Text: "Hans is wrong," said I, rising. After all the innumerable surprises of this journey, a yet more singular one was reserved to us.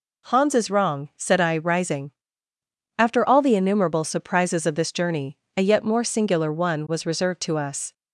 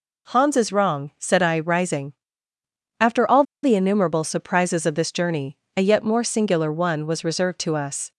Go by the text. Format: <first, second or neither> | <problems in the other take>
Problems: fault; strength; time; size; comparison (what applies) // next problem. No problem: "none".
first | pauses between "all" and "the"; slight; at 3.4 s; 0.20 s long